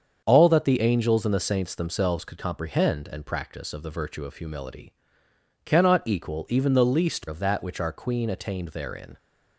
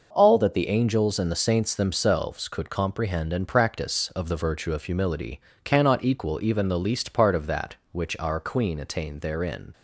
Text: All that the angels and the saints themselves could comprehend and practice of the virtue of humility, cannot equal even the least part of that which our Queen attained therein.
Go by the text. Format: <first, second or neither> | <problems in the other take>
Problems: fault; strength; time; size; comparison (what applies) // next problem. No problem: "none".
second | starts louder than the rest; until 1.2 s; 7 dB // skips "part"; at 7.2 s